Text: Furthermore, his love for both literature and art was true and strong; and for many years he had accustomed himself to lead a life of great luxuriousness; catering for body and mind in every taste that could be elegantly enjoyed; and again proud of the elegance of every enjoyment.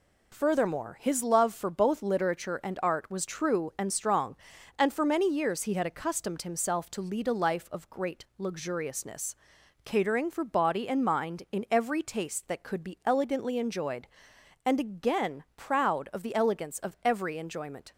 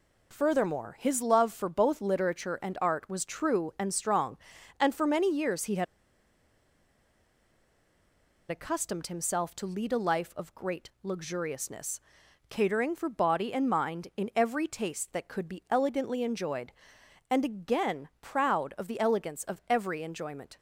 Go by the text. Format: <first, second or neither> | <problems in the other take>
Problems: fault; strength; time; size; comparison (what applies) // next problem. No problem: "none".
first | pauses between "had" and "accustomed"; strong; at 5.8 s; 2.6 s long